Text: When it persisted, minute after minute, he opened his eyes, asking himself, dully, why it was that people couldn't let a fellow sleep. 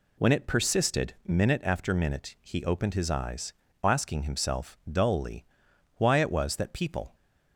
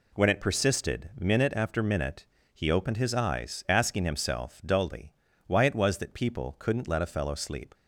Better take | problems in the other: second | stops before "couldn't let a fellow sleep"; at 7.1 s

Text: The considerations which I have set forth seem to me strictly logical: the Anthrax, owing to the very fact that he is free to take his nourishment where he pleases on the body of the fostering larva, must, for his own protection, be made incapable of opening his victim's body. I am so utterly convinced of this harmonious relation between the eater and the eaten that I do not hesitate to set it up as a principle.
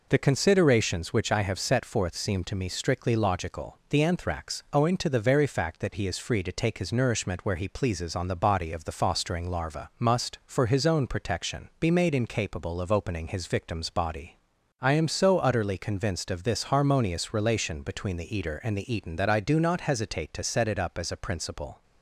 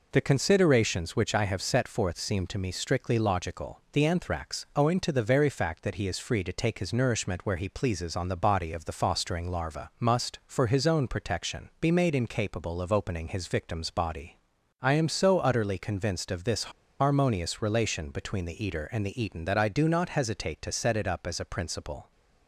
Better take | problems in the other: first | pauses between "this" and "harmonious"; slight; at 16.7 s; 0.30 s long

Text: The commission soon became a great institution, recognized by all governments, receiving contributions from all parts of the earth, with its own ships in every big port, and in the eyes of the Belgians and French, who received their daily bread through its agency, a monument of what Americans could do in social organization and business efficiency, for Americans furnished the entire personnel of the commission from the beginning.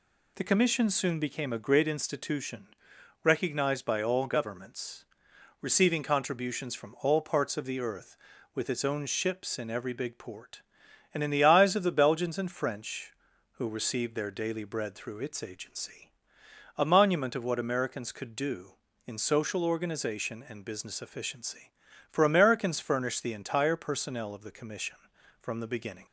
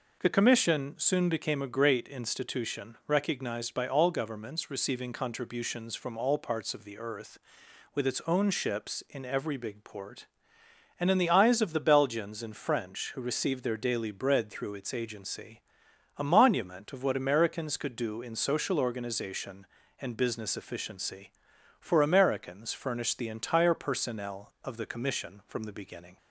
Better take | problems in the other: neither | none

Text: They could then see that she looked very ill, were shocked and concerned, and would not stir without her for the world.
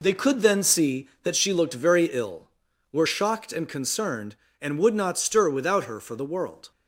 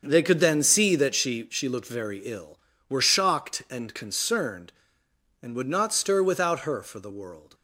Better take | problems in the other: first | starts louder than the rest; until 1.0 s; 6.5 dB // says "she" twice; at 1.4 s

